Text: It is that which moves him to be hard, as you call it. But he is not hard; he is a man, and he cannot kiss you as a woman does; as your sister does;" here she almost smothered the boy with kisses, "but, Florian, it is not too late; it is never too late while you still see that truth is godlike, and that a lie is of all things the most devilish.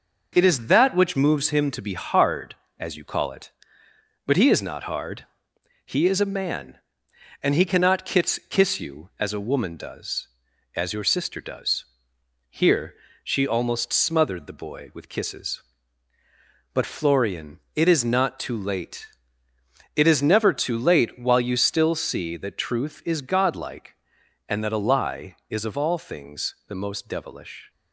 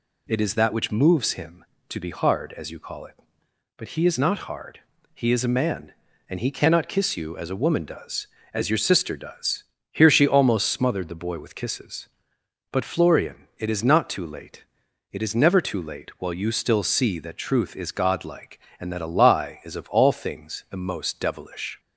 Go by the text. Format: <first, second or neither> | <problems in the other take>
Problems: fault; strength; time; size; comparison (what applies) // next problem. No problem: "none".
second | says "kiss" twice; at 8.4 s // pauses between "here" and "she"; slight; at 12.9 s; 0.26 s long